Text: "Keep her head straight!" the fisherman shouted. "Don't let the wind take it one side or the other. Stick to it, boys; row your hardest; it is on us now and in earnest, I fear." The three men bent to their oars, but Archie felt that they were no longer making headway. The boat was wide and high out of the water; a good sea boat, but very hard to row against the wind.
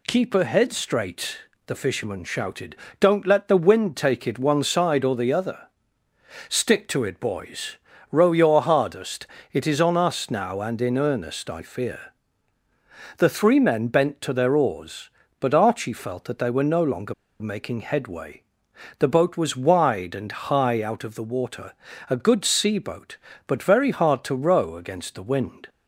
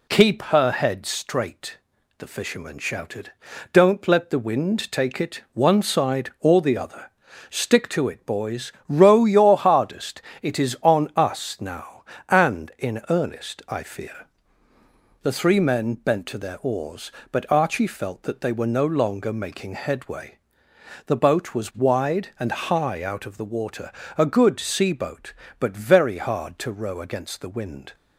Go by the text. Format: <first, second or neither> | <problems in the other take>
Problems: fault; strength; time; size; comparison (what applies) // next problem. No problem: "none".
second | pauses between "longer" and "making"; slight; at 17.1 s; 0.26 s long